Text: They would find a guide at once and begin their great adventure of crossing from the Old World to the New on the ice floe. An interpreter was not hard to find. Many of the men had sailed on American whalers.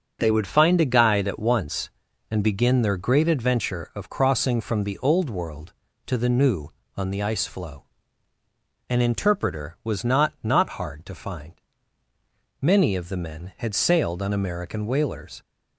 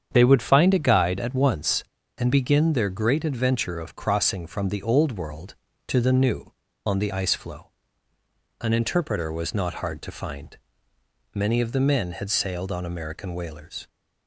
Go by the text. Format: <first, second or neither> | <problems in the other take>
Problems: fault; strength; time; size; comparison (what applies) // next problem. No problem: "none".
second | starts louder than the rest; until 1.2 s; 6.5 dB; strong in the second // says "not" twice; at 10.4 s